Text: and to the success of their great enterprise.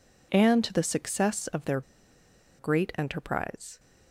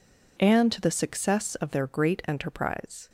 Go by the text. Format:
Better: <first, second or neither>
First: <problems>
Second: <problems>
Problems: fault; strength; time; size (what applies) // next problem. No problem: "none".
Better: second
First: pauses between "their" and "great"; noticeable; at 1.8 s; 0.77 s long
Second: none